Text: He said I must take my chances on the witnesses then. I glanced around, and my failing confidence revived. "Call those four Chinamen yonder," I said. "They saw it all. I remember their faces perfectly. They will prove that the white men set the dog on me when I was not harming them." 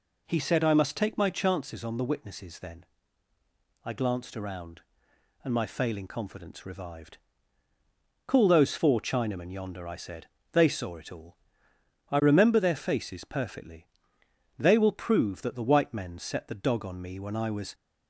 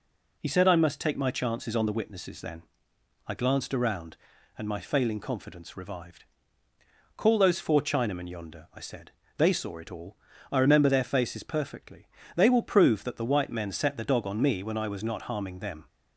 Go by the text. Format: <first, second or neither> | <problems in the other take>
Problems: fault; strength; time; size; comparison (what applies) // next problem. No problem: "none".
second | stops before "not harming them"; at 17.7 s